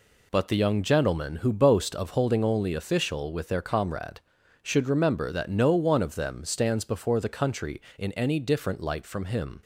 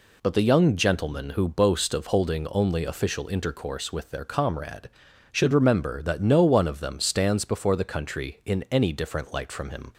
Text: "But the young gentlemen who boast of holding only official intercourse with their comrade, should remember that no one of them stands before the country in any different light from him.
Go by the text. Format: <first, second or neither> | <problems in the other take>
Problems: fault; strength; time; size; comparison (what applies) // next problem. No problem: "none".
second | skips "intercourse"; at 3.3 s